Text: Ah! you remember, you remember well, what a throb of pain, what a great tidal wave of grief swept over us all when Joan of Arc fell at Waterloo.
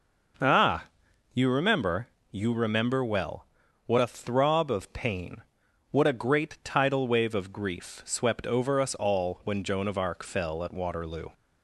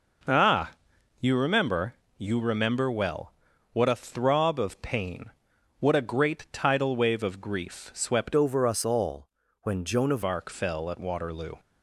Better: first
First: none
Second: changes voice from "over" to "of"; from 8.3 to 10.2 s; 1.9 s long // pauses between "all" and "when"; slight; at 9.2 s; 0.32 s long

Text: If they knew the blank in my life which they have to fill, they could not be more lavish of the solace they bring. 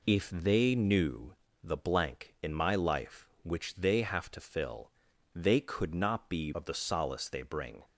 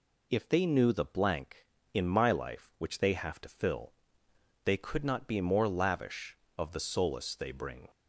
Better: second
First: pauses between "knew" and "the"; slight; at 1.3 s; 0.26 s long // skips "more lavish"; at 6.5 s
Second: none

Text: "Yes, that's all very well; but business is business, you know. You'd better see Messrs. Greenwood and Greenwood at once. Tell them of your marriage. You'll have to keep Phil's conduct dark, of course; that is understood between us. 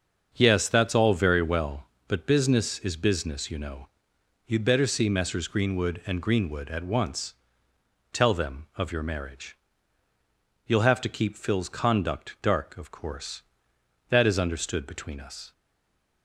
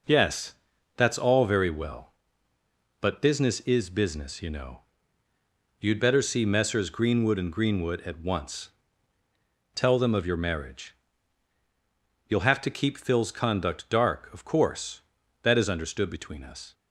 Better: second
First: starts louder than the rest; until 1.3 s; 6.5 dB // stays silent after the last word; slight; from 15.5 s on; 0.7 s long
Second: none

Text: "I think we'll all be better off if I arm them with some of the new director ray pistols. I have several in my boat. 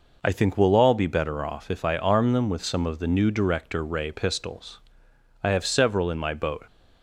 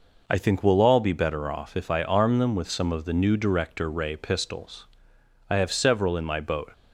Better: neither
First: none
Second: none

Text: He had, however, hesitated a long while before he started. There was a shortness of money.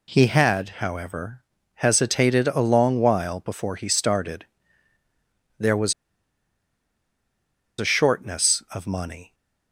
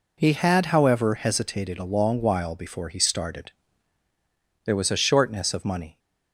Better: second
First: pauses between "was" and "a"; strong; at 5.9 s; 1.8 s long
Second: none

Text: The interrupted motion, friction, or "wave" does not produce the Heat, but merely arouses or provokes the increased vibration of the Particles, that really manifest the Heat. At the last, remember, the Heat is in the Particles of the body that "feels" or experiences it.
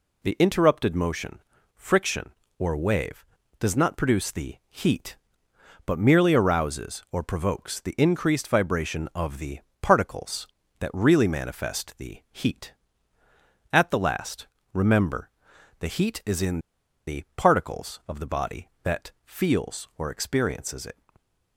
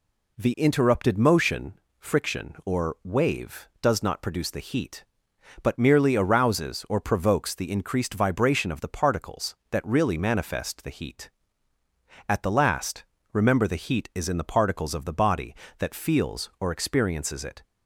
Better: second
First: pauses between "the" and "Particles"; slight; at 9.5 s; 0.22 s long // pauses between "in" and "the"; noticeable; at 16.5 s; 0.47 s long // stays silent after the last word; slight; from 20.9 s on; 0.6 s long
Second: none

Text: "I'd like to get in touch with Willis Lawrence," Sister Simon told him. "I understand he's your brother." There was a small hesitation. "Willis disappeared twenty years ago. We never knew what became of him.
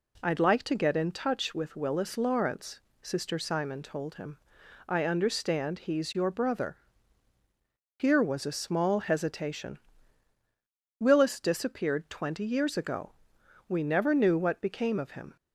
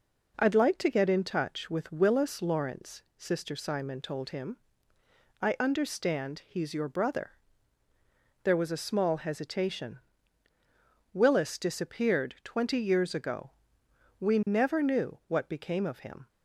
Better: second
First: says "Here" for "There"; at 7.9 s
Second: none

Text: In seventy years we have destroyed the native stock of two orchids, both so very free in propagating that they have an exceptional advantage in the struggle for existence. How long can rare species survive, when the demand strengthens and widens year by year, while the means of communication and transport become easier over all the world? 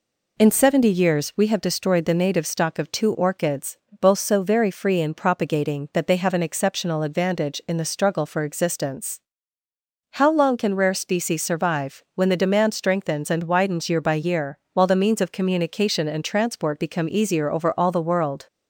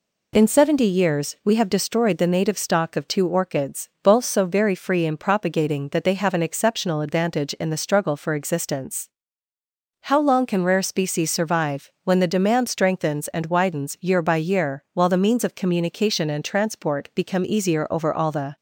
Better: first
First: none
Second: stops before "world"; at 18.5 s

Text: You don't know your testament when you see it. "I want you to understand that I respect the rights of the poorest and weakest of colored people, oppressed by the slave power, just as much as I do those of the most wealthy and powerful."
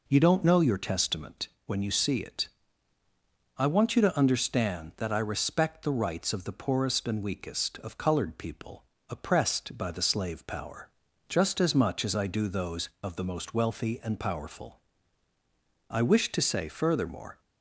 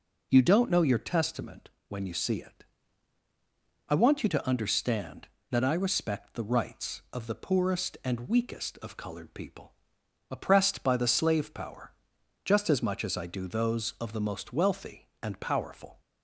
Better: second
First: pauses between "testament" and "when"; slight; at 1.4 s; 0.18 s long // goes on to say "I wish to say furthermore"; from 15.8 s on; 1.5 s long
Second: pauses between "testament" and "when"; slight; at 1.6 s; 0.18 s long

